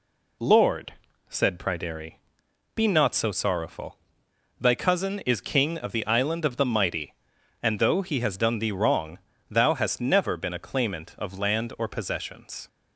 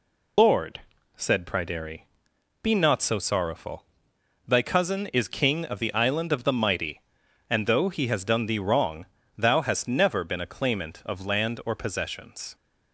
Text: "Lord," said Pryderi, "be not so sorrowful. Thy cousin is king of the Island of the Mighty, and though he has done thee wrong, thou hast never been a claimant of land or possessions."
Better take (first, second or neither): first